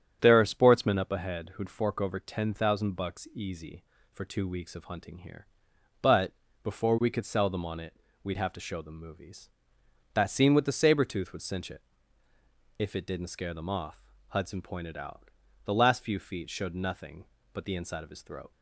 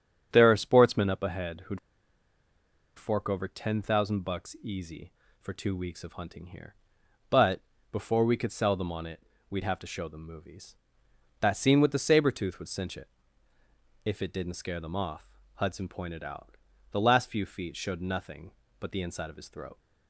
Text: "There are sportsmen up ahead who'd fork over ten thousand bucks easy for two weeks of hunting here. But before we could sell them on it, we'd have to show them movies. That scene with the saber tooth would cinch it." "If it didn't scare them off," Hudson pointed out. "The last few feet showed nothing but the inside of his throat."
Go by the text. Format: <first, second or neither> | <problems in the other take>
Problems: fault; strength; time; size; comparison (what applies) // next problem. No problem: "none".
first | starts louder than the rest; strong; until 1.3 s; 9 dB; strong in the first // pauses between "who'd" and "fork"; at 1.7 s; 1.1 s long // pauses between "But" and "before"; slight; at 7.6 s; 0.28 s long; slight in the first